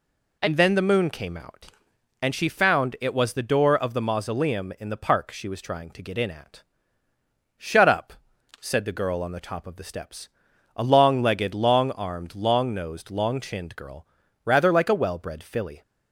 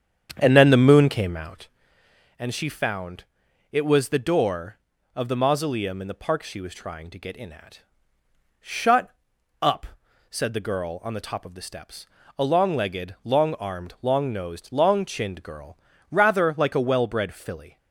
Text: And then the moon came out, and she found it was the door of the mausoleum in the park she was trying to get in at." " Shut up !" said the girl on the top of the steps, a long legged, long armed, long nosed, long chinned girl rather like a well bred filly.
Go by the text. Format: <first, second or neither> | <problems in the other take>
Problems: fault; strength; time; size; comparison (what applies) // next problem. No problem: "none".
first | starts louder than the rest; strong; until 1.8 s; 8.5 dB // pauses between "found" and "it"; noticeable; at 3.2 s; 0.46 s long // pauses between "Shut" and "up"; noticeable; at 9.1 s; 0.50 s long // pauses between "girl" and "rather"; slight; at 15.7 s; 0.36 s long; also in the first